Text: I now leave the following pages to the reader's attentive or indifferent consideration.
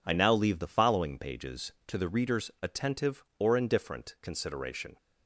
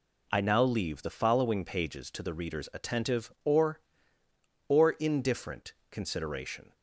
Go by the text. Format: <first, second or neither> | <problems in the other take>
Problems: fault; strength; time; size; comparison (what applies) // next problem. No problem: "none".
first | says "or" twice; at 4.6 s // pauses between "indifferent" and "consideration"; slight; at 5.7 s; 0.18 s long